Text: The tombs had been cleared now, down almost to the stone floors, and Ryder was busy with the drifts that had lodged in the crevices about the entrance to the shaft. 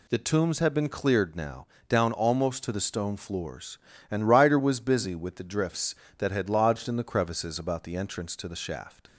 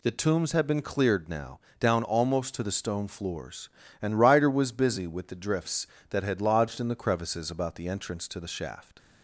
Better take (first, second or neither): neither